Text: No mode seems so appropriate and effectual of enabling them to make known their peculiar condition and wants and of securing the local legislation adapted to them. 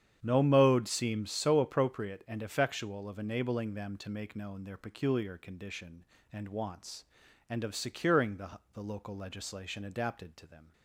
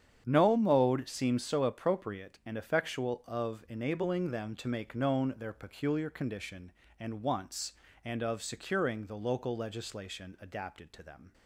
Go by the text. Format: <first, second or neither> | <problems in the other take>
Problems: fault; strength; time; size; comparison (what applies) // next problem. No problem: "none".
second | starts louder than the rest; strong; until 1.2 s; 9 dB; strong in the second // says "the" twice; at 8.7 s